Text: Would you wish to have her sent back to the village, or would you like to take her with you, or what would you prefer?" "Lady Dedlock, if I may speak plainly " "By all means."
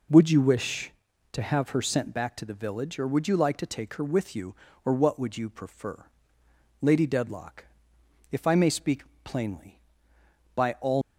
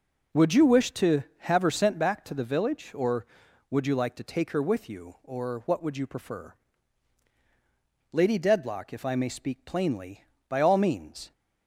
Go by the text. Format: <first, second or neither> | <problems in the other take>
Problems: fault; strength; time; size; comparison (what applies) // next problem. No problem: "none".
second | pauses between "speak" and "plainly"; slight; at 9.0 s; 0.20 s long // stops before "means"; at 11.0 s